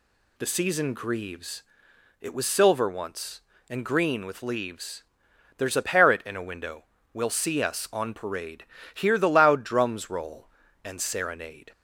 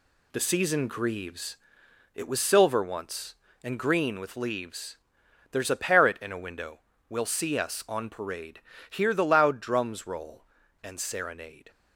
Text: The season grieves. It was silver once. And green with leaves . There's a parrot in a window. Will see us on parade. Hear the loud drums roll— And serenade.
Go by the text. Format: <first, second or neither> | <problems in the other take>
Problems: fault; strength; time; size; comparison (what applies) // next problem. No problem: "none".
first | gets quieter; throughout; 7 dB